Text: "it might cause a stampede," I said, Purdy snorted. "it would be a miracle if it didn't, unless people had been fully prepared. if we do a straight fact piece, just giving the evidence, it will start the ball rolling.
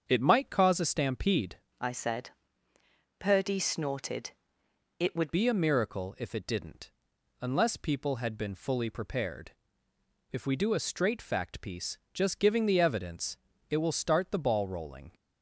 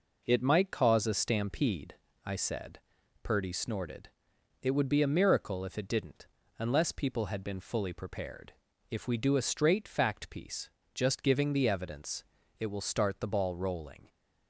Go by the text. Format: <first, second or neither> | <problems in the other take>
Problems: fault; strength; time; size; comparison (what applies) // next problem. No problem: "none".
second | starts louder than the rest; strong; until 1.0 s; 7 dB // changes voice from "I" to "would"; from 1.8 to 5.3 s; 3.5 s long